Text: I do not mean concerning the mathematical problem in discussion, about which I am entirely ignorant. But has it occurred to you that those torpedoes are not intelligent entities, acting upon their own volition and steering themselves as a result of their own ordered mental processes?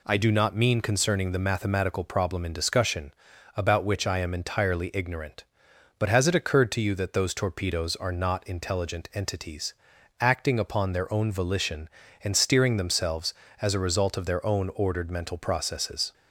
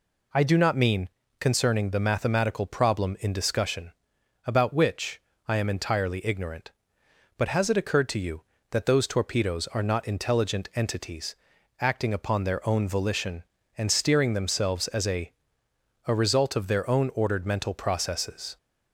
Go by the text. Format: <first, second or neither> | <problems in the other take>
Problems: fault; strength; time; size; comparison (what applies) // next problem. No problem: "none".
first | pauses between "mean" and "concerning"; slight; at 1.0 s; 0.30 s long // pauses between "which" and "I"; slight; at 5.2 s; 0.26 s long // says "a" twice; at 16.0 s